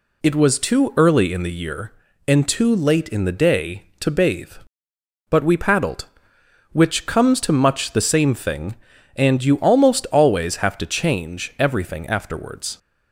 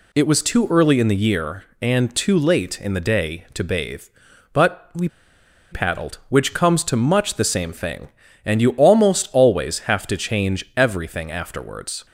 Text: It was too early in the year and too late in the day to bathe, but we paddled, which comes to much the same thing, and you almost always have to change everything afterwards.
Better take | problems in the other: first | pauses between "we" and "paddled"; noticeable; at 5.0 s; 0.63 s long

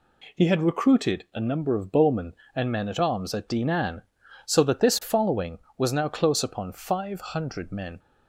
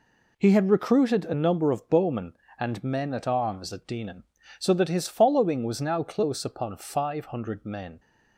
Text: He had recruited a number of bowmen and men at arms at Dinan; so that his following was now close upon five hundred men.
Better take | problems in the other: second | says "this" for "his"; at 4.7 s

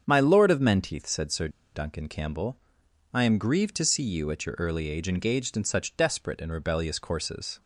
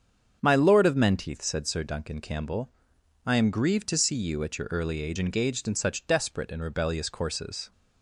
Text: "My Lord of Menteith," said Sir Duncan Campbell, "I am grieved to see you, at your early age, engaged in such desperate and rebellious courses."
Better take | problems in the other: second | starts louder than the rest; strong; until 1.0 s; 7.5 dB; strong in the second // pauses between "Sir" and "Duncan"; slight; at 1.4 s; 0.25 s long

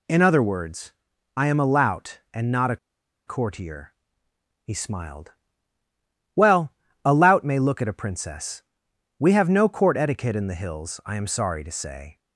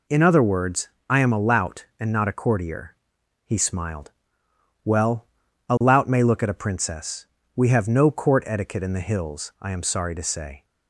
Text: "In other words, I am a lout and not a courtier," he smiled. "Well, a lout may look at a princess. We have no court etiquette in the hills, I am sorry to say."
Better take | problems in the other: second | pauses between "a" and "courtier"; noticeable; at 2.7 s; 0.50 s long

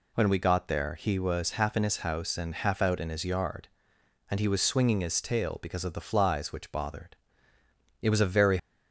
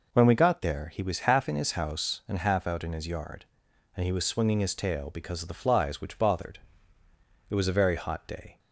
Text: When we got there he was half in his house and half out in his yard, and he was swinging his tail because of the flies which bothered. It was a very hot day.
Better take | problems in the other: second | stops before "hot day"; at 8.5 s

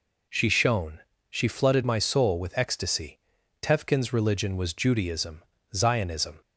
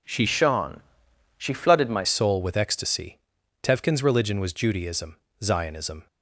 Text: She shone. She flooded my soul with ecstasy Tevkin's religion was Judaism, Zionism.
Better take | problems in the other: first | changes voice from "shone" to "my"; from 0.2 to 2.0 s; 1.8 s long // pauses between "ecstasy" and "Tevkin's"; at 3.1 s; 0.44 s long; also in the first

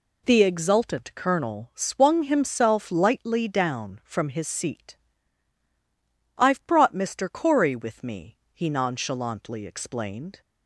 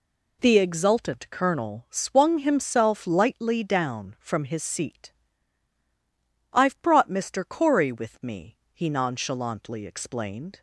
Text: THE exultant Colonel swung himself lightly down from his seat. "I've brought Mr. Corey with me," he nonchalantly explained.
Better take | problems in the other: neither | none

